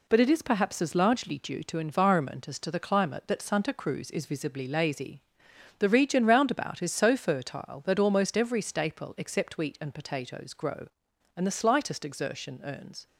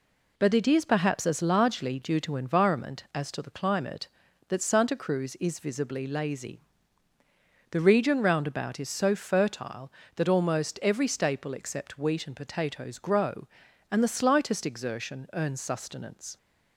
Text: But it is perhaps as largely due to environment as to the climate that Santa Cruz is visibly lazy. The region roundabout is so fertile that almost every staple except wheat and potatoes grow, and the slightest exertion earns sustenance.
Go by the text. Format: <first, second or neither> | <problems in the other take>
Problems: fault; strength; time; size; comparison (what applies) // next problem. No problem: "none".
second | stops before "sustenance"; at 13.0 s